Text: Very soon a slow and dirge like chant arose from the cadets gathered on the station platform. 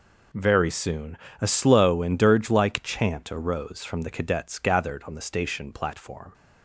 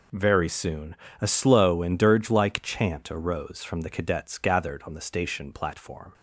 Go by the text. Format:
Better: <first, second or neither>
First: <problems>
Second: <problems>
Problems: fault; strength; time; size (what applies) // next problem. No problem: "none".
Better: neither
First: pauses between "soon" and "a"; slight; at 1.1 s; 0.22 s long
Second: pauses between "soon" and "a"; slight; at 0.9 s; 0.24 s long